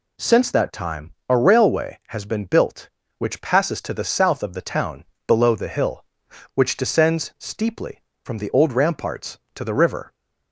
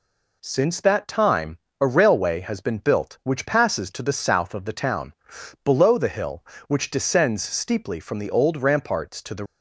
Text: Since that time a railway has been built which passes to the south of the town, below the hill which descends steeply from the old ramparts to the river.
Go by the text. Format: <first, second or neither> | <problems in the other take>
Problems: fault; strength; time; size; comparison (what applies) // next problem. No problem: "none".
first | pauses between "time" and "a"; slight; at 1.5 s; 0.24 s long; slight in the first // stops before "river"; at 9.4 s